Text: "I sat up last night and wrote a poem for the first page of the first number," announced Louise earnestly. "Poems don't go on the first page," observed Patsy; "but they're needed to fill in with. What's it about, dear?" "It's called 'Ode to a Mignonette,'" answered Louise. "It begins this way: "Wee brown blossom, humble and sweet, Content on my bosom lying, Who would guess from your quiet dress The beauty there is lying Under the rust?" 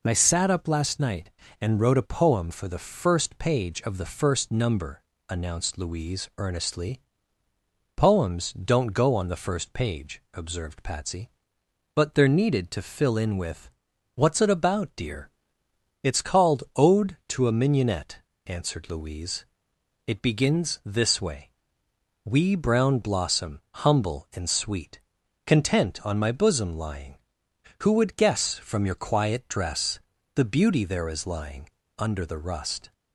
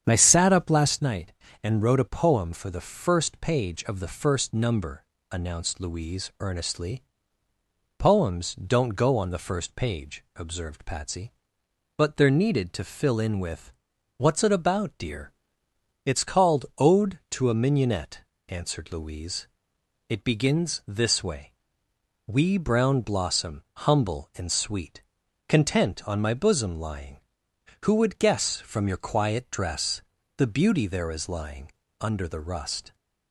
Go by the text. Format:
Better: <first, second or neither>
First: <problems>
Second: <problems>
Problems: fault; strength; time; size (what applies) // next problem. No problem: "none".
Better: first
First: pauses between "dress" and "The"; slight; at 29.9 s; 0.36 s long // pauses between "lying" and "Under"; slight; at 31.6 s; 0.30 s long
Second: starts louder than the rest; strong; until 1.1 s; 8.5 dB // pauses between "dress" and "The"; slight; at 30.0 s; 0.36 s long // pauses between "lying" and "Under"; slight; at 31.7 s; 0.30 s long